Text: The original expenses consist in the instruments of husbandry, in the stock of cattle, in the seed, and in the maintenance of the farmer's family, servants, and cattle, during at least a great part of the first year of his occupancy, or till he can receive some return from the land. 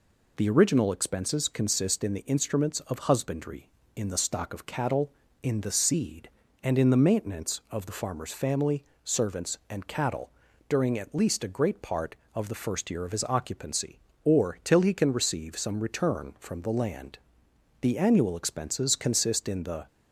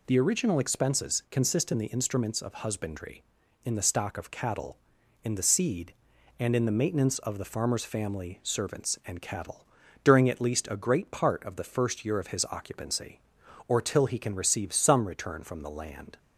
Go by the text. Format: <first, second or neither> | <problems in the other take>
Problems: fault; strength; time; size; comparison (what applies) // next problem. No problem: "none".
second | goes on to say "The annual expenses consist in the"; strong; from 17.8 s on; 2.0 s long